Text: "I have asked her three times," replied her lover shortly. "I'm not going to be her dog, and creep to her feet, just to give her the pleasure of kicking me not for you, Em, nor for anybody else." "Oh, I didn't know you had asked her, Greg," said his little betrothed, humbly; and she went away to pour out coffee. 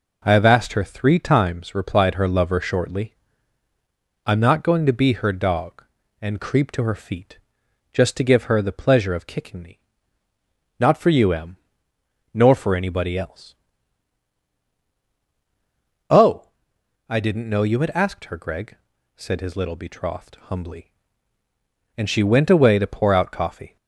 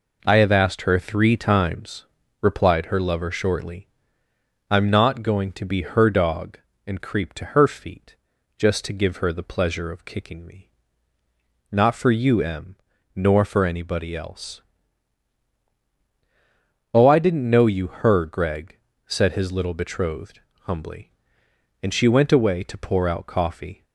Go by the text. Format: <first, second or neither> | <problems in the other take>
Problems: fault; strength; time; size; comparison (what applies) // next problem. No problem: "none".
first | pauses between "me" and "not"; at 10.6 s; 1.0 s long; also in the first // skips "had asked"; at 17.8 s